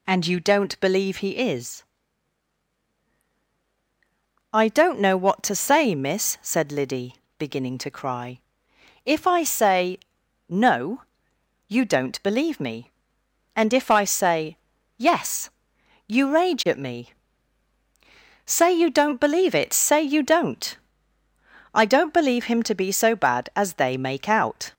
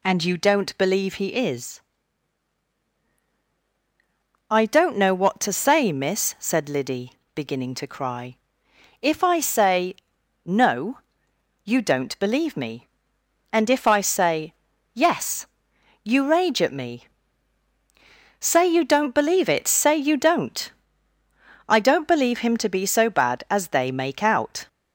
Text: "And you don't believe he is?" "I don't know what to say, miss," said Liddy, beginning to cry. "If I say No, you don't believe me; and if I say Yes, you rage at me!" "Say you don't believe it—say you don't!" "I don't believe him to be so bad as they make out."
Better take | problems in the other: neither | pauses between "say" and "No"; noticeable; the same in both // pauses between "say" and "Yes"; the same in both

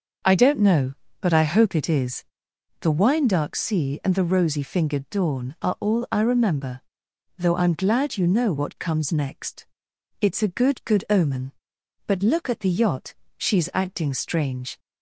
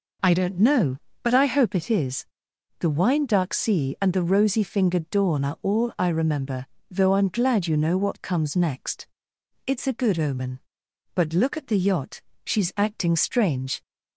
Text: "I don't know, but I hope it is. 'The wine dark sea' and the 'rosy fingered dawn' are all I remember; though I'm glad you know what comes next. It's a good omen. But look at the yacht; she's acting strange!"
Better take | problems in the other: second | starts louder than the rest; until 1.5 s; 6 dB // says "good" twice; at 10.8 s

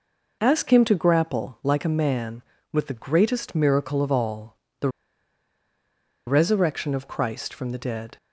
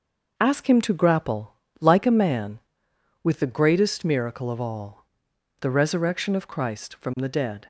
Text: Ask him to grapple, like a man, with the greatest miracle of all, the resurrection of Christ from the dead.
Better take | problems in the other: second | pauses between "the" and "resurrection"; strong; at 4.8 s; 1.3 s long

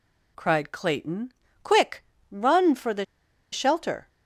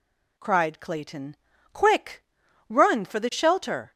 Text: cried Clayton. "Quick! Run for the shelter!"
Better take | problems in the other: second | pauses between "the" and "shelter"; noticeable; at 3.0 s; 0.47 s long

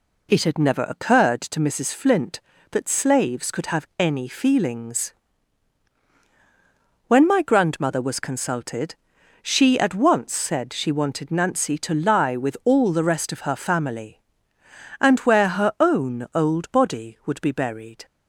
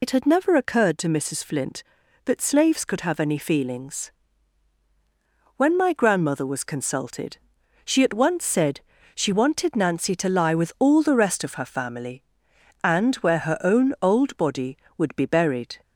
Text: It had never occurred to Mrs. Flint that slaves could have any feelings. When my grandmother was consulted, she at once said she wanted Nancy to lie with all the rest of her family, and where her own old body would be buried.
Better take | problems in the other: first | loses the start of "It"; at 0.0 s; 70 ms // pauses between "said" and "she"; slight; at 8.7 s; 0.36 s long

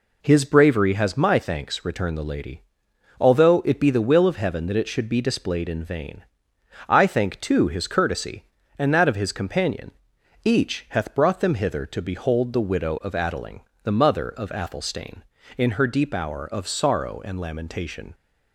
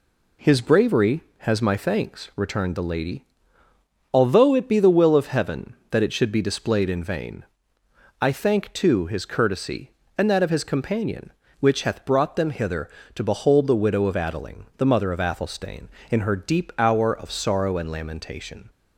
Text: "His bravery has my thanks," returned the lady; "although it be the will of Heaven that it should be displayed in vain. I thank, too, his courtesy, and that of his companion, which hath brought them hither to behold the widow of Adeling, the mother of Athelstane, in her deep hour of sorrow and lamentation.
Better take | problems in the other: second | says "each" for "which"; at 10.4 s

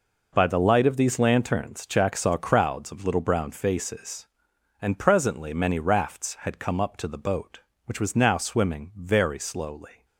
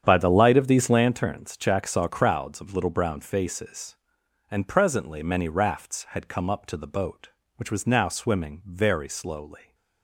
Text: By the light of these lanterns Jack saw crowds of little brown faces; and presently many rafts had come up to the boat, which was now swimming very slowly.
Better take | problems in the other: first | starts louder than the rest; strong; until 1.0 s; 8.5 dB

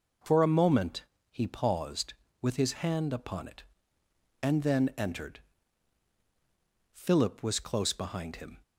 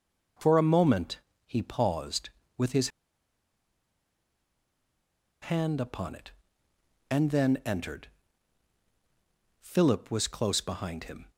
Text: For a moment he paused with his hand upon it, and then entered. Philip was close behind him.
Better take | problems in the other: first | pauses between "moment" and "he"; slight; at 1.1 s; 0.28 s long; slight in the first // pauses between "his" and "hand"; strong; at 2.8 s; 2.5 s long

